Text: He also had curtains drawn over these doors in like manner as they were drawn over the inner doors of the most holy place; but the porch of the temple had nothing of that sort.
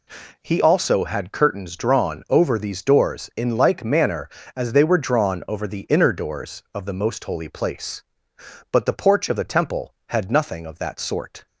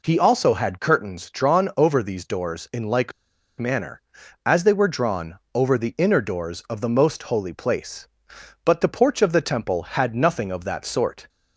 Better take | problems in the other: first | pauses between "like" and "manner"; noticeable; at 3.1 s; 0.46 s long // pauses between "drawn" and "over"; slight; at 5.3 s; 0.16 s long

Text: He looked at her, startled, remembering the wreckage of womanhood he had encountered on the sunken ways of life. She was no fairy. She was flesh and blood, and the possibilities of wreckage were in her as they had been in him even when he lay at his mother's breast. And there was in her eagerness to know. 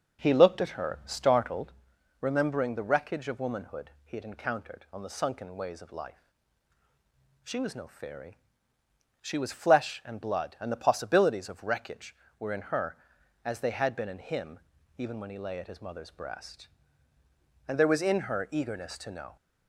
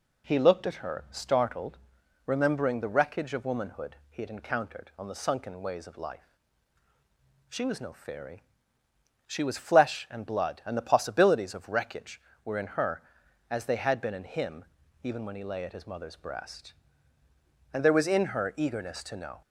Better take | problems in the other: second | starts louder than the rest; noticeable; until 1.8 s; 6 dB // pauses between "him" and "even"; at 14.5 s; 0.38 s long; also in the second

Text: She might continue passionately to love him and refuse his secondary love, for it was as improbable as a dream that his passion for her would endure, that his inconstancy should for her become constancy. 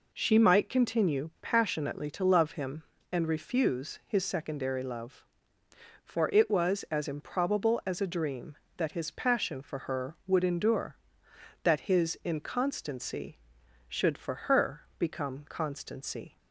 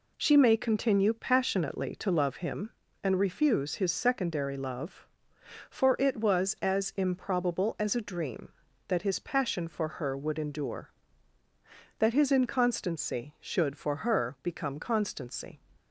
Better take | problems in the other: first | says "may" for "might"; at 0.3 s

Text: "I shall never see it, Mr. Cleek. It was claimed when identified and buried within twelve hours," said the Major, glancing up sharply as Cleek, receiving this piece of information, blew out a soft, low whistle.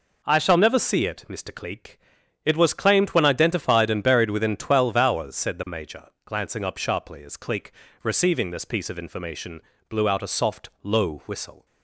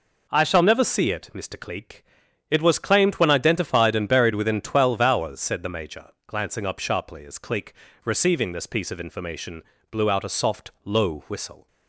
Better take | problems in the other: neither | none

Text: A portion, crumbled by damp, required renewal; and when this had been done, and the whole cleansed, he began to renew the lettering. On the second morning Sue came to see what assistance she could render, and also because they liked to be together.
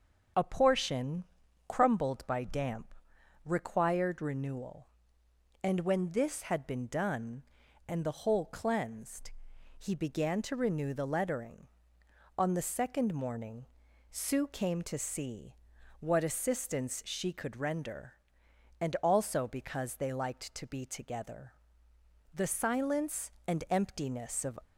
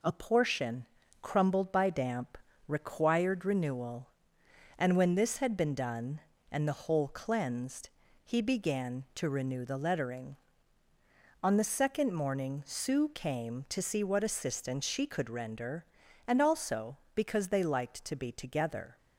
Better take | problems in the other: second | starts louder than the rest; noticeable; until 1.7 s; 6 dB // pauses between "morning" and "Sue"; noticeable; at 13.6 s; 0.46 s long // pauses between "see" and "what"; at 15.5 s; 0.44 s long // goes on to say "The silence and emptiness of"; strong; from 22.3 s on; 2.2 s long

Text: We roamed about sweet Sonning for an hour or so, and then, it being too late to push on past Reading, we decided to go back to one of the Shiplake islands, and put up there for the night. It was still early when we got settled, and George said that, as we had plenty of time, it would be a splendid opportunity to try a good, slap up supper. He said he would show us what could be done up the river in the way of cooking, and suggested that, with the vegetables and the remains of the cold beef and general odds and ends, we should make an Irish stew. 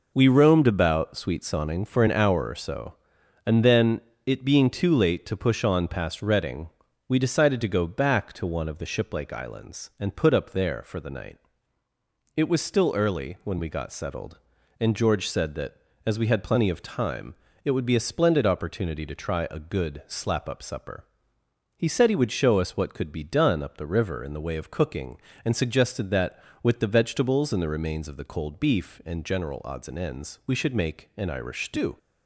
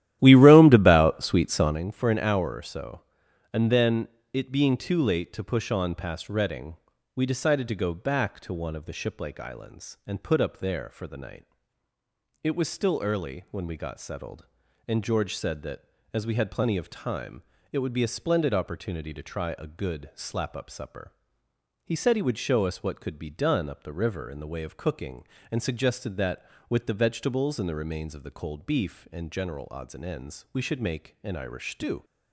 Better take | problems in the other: first | starts louder than the rest; strong; until 1.8 s; 13 dB

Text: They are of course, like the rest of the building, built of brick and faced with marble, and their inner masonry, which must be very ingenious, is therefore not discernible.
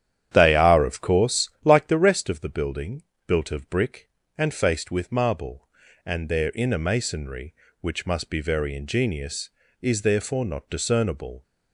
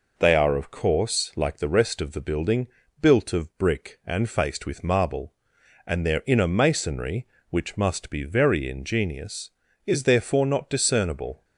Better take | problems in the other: second | starts louder than the rest; strong; until 2.0 s; 10 dB

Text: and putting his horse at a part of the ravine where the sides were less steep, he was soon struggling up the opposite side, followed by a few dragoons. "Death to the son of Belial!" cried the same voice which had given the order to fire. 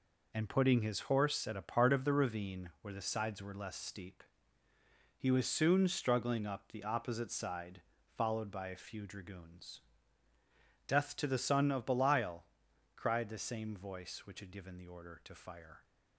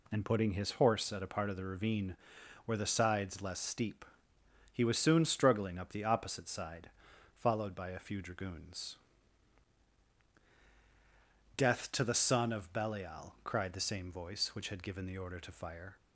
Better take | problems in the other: first | pauses between "ravine" and "where"; noticeable; at 2.1 s; 0.50 s long // skips "were"; at 3.4 s

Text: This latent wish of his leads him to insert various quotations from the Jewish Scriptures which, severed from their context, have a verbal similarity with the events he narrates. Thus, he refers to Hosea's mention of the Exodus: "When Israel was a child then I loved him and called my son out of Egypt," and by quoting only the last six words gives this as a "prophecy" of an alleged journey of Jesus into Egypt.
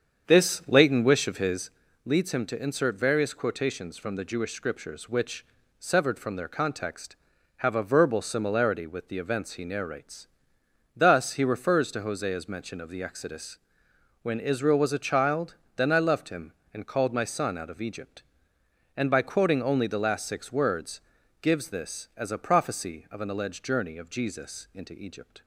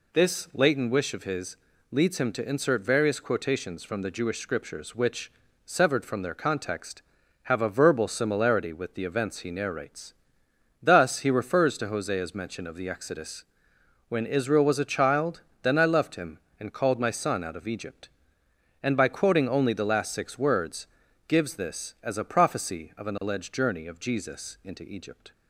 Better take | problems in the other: second | starts louder than the rest; strong; until 1.9 s; 7.5 dB // pauses between "his" and "leads"; slight; at 1.6 s; 0.34 s long; slight in the second // pauses between "child" and "then"; slight; at 15.5 s; 0.18 s long; slight in the second // pauses between "words" and "gives"; at 21.0 s; 0.42 s long; also in the second

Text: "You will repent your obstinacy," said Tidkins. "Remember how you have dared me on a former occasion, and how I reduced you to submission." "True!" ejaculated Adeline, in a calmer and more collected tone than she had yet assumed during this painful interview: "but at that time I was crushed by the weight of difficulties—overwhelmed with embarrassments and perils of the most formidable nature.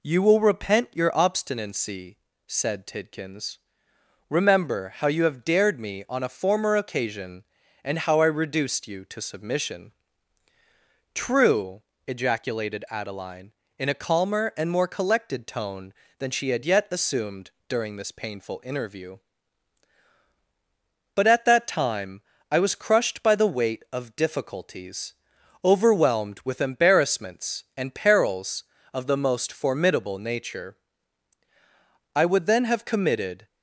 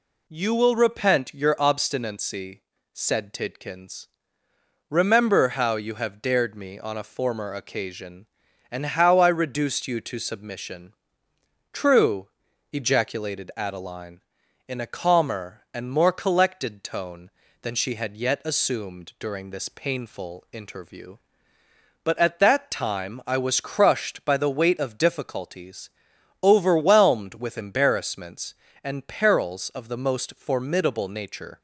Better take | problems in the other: second | pauses between "assumed" and "during"; slight; at 17.5 s; 0.18 s long // pauses between "time" and "I"; slight; at 22.2 s; 0.28 s long // goes on to say "I would then have committed"; from 32.1 s on; 1.3 s long

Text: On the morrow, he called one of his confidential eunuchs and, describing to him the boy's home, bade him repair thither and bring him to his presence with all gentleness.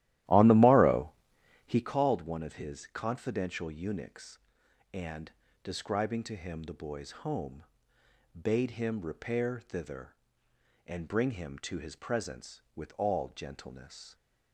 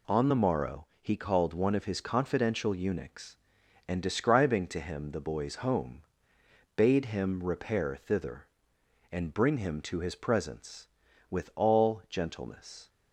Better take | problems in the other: second | starts louder than the rest; strong; until 2.0 s; 14 dB

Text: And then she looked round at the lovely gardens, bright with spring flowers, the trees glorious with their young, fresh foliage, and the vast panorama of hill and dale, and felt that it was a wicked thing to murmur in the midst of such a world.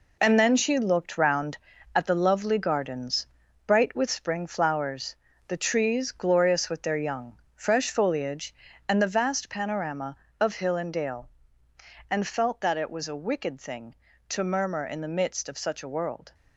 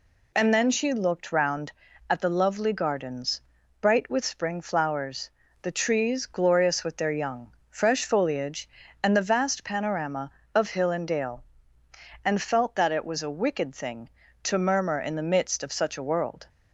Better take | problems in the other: second | gets quieter; strong; throughout; 8 dB

